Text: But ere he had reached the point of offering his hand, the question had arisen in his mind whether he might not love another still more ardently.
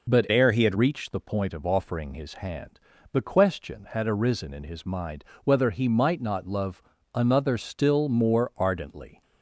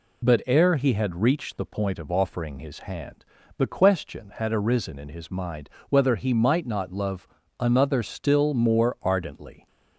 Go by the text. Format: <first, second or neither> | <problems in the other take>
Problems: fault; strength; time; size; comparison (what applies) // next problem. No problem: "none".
second | changes voice from "ere" to "had"; from 0.3 to 0.7 s; 0.4 s long // pauses between "mind" and "whether"; slight; at 5.2 s; 0.22 s long; slight in the second // pauses between "love" and "another"; slight; at 6.8 s; 0.32 s long; slight in the second